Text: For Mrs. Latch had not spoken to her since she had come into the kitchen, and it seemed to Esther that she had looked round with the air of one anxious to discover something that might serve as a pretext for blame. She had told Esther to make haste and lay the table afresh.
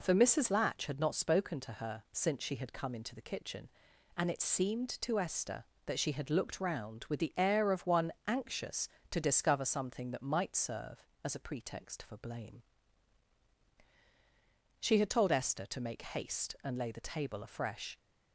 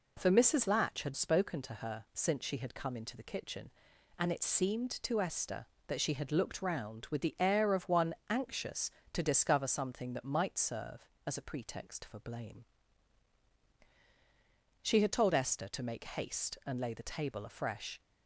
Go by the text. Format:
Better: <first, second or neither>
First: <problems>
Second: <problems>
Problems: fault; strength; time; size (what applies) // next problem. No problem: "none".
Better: first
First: pauses between "one" and "anxious"; slight; at 8.1 s; 0.16 s long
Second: skips "not"; at 1.1 s // pauses between "one" and "anxious"; slight; at 8.1 s; 0.16 s long